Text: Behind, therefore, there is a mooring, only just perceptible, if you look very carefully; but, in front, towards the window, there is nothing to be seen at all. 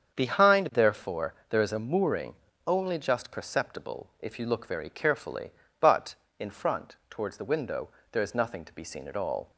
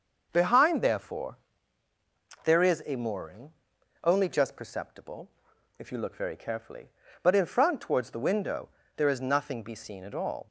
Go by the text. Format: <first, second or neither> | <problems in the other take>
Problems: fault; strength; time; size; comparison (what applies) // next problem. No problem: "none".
first | starts louder than the rest; noticeable; until 1.3 s; 6 dB; strong in the first // skips "to"; at 9.6 s